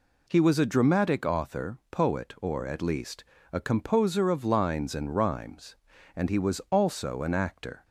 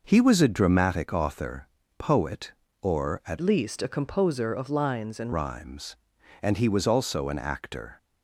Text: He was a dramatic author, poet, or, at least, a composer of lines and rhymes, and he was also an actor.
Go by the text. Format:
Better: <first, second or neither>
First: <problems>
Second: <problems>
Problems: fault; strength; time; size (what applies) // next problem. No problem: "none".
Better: first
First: none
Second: changes voice from "least" to "and"; from 3.4 to 5.3 s; 1.9 s long